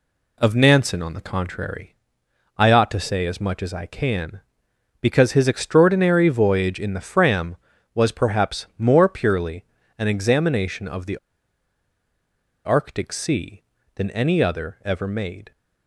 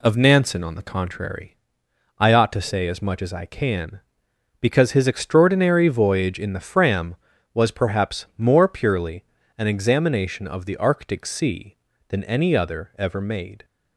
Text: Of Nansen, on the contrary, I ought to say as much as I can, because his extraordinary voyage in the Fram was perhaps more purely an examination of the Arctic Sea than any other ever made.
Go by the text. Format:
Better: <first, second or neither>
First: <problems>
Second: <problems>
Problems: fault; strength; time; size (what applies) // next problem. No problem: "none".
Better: second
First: pauses between "purely" and "an"; slight; at 9.6 s; 0.32 s long // pauses between "the" and "Arctic"; strong; at 11.1 s; 1.4 s long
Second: pauses between "purely" and "an"; slight; at 9.2 s; 0.32 s long